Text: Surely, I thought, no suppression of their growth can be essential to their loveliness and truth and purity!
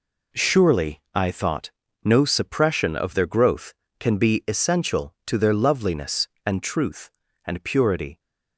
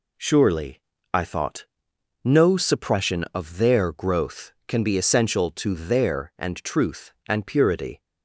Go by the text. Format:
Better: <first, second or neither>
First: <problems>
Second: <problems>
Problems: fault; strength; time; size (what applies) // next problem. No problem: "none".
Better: first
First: none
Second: skips "loveliness"; at 6.3 s